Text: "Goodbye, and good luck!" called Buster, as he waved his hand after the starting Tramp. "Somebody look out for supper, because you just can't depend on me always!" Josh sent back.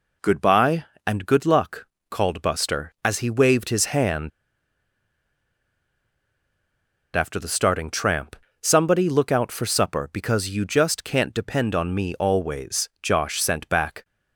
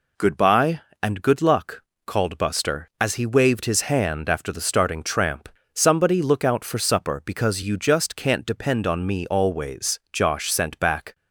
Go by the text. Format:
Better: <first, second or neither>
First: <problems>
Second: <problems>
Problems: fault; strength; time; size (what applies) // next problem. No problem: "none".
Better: second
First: pauses between "hand" and "after"; strong; at 4.3 s; 2.8 s long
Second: none